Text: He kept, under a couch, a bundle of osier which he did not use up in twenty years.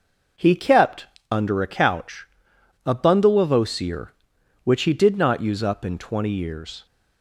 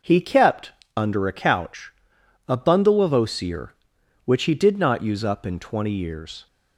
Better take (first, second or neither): neither